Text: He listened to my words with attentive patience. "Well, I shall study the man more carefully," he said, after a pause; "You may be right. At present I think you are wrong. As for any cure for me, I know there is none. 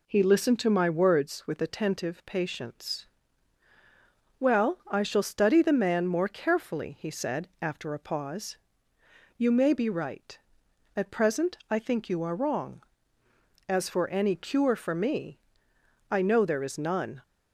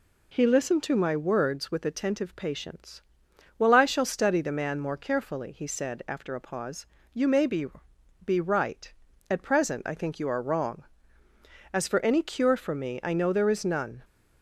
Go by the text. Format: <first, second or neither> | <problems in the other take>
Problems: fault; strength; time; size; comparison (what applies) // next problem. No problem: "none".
first | says "be" twice; at 8.2 s